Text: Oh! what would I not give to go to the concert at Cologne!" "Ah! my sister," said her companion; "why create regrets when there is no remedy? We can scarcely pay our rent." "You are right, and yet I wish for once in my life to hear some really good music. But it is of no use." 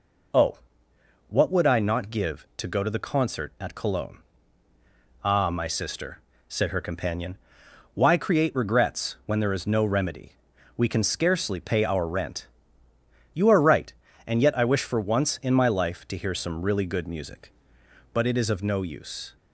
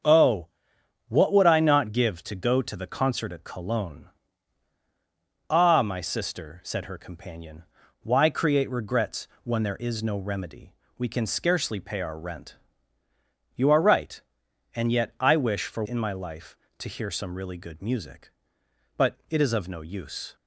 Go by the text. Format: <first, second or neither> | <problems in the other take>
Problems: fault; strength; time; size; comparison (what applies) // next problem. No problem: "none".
first | starts louder than the rest; until 1.6 s; 7 dB // pauses between "regrets" and "when"; slight; at 9.2 s; 0.16 s long // skips "once"; at 15.8 s